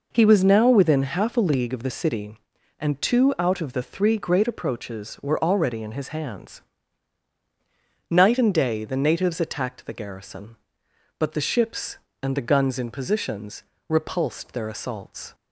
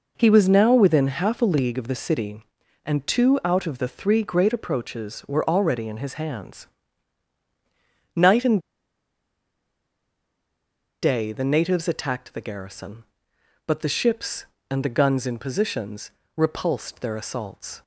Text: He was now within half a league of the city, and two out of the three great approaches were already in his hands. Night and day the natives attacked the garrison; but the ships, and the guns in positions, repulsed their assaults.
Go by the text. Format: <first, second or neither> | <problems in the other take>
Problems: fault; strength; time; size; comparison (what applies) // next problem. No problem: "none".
first | pauses between "and" and "day"; strong; at 8.6 s; 2.4 s long